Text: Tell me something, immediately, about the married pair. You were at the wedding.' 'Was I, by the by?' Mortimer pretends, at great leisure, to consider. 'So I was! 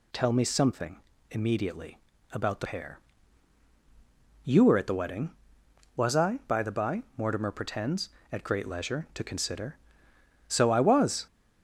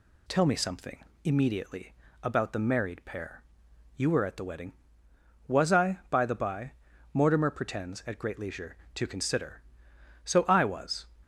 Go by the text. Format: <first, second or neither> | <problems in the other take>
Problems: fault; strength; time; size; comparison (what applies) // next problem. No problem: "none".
second | skips "married"; at 2.6 s